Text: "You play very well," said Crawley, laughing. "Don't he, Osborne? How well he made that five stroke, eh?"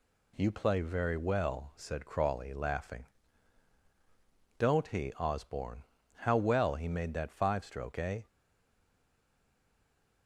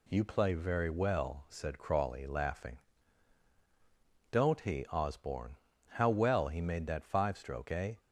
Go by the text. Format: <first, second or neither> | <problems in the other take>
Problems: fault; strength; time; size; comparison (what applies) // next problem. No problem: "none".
second | stays silent after the last word; noticeable; from 8.2 s on; 2.0 s long